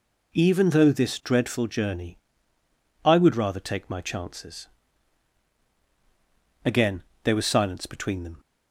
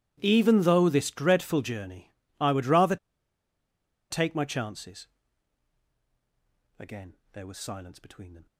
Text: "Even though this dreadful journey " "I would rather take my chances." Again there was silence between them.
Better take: first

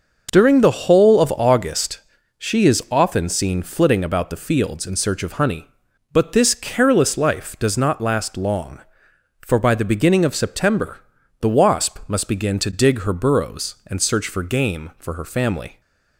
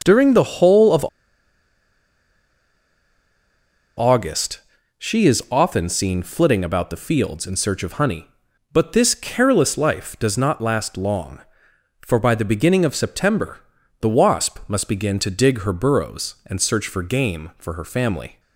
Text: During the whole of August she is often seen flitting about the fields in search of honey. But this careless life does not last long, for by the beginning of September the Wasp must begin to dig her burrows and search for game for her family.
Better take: first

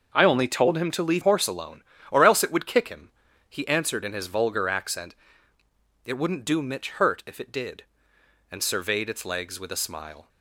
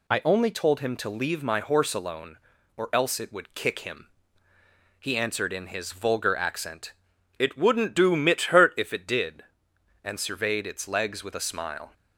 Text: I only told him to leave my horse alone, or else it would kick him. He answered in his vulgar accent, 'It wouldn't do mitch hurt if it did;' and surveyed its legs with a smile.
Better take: second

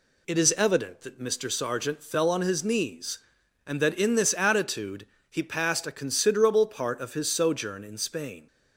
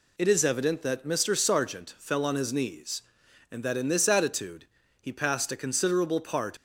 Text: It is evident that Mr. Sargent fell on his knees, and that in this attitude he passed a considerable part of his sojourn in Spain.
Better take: first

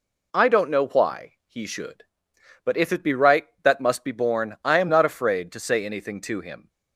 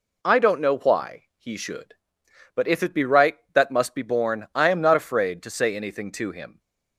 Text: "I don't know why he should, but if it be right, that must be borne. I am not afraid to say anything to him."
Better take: neither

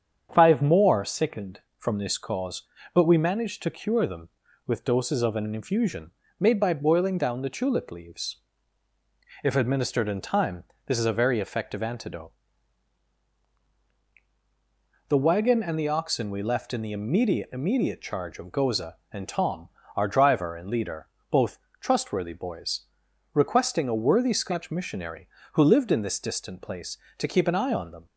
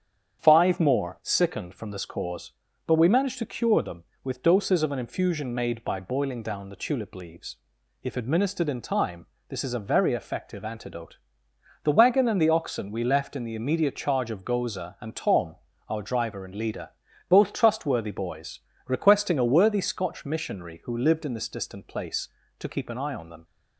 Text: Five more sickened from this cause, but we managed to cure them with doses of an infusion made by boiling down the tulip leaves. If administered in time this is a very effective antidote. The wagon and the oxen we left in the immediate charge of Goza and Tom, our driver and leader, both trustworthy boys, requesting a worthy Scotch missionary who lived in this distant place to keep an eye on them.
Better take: second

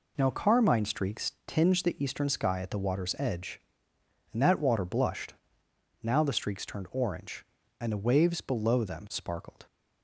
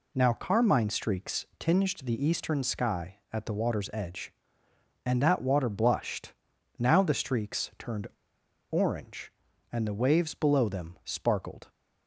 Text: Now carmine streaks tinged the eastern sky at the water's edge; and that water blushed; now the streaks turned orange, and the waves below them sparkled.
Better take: first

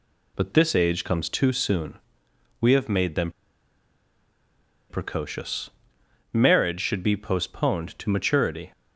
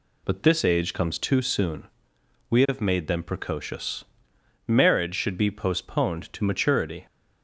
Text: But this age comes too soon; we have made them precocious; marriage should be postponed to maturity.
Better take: second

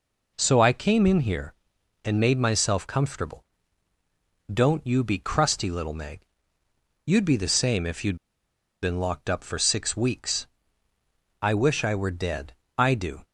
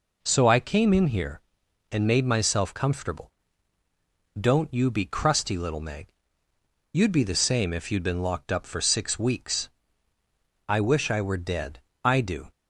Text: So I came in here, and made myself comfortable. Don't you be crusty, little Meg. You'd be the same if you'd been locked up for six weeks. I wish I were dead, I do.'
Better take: second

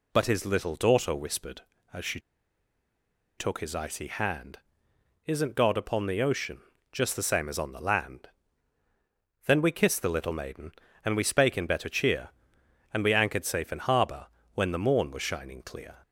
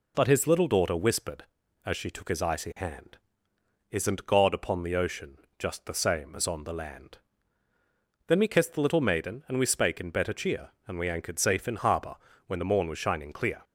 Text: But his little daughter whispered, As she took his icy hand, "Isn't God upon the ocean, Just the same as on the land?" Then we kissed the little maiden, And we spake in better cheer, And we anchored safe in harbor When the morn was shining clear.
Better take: second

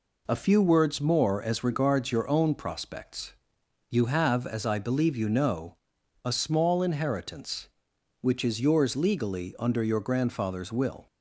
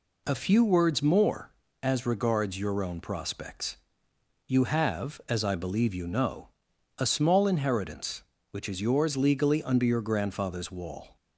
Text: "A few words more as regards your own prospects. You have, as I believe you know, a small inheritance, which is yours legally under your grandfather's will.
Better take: first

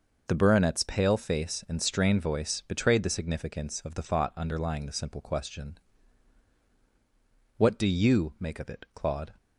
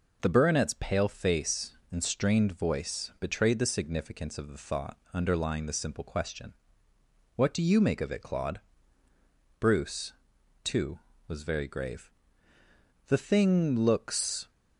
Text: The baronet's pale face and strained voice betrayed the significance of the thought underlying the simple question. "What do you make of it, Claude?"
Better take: first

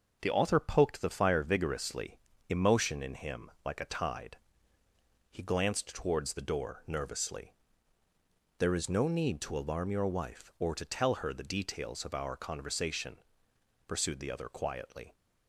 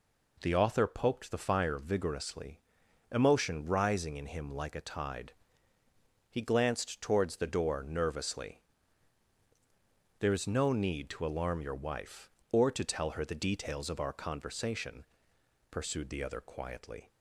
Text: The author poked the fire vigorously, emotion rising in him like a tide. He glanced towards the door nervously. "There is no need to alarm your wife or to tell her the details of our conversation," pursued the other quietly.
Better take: second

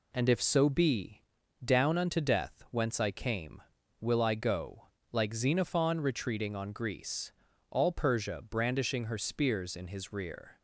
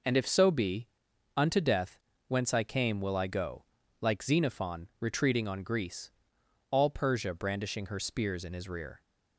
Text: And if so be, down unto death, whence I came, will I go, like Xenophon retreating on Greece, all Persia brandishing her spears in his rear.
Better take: first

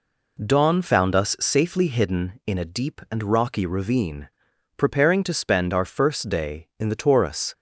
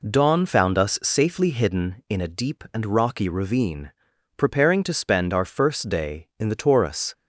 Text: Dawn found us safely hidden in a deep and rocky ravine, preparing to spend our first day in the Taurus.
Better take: neither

